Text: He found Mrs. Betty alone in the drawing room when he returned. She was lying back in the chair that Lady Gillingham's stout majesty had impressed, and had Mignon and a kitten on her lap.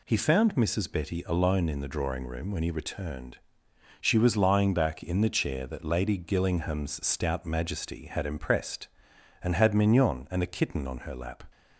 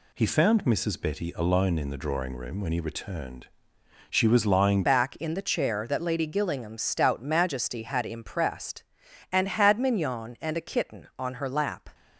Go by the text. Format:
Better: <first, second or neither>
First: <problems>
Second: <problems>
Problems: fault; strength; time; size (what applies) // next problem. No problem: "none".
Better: first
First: none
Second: changes voice at "back"; from 4.8 s on; 7.1 s long